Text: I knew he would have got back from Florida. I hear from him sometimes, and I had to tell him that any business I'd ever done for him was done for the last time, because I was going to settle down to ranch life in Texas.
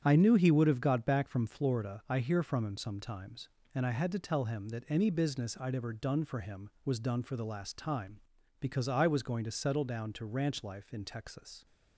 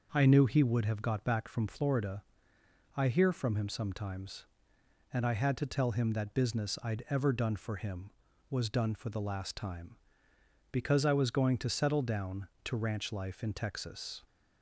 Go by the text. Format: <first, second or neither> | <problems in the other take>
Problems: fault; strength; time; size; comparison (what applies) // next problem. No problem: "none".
first | starts louder than the rest; noticeable; until 1.1 s; 6 dB; strong in the first // skips "any"; at 6.3 s